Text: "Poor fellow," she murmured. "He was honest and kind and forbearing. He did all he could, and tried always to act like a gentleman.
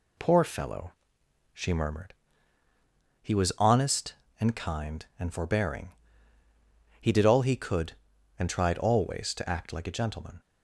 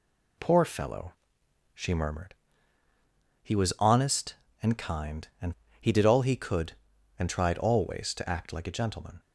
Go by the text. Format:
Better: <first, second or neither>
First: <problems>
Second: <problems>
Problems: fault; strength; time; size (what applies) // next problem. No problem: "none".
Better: first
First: none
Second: skips "forbearing"; at 5.6 s